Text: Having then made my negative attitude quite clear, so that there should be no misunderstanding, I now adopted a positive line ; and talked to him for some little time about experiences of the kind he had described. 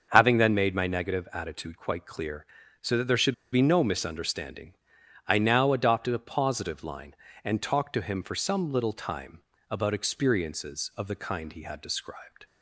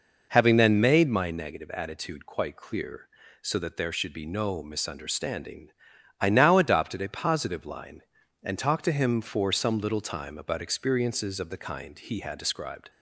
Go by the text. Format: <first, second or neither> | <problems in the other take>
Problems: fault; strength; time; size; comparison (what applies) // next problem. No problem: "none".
second | starts louder than the rest; until 1.1 s; 6.5 dB // pauses between "should" and "be"; slight; at 3.3 s; 0.18 s long // pauses between "time" and "about"; slight; at 9.3 s; 0.30 s long